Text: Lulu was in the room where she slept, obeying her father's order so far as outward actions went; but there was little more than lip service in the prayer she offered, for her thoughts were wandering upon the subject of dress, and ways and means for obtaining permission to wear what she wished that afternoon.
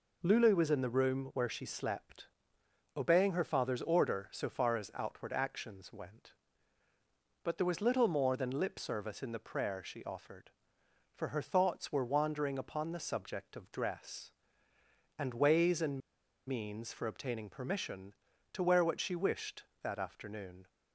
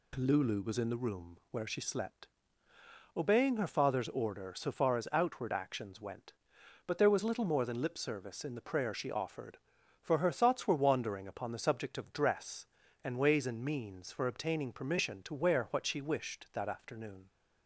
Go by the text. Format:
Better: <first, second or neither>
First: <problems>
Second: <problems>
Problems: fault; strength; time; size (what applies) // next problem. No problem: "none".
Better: second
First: pauses between "and" and "means"; noticeable; at 16.0 s; 0.49 s long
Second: none